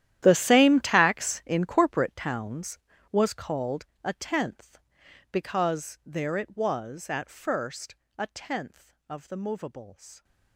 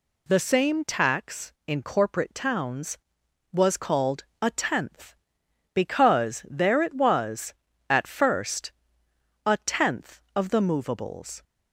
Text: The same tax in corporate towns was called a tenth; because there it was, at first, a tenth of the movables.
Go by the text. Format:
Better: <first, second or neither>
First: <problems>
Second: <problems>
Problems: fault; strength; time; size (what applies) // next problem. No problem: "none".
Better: second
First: gets quieter; strong; throughout; 18 dB // pauses between "called" and "a"; slight; at 3.8 s; 0.22 s long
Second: pauses between "called" and "a"; slight; at 4.2 s; 0.16 s long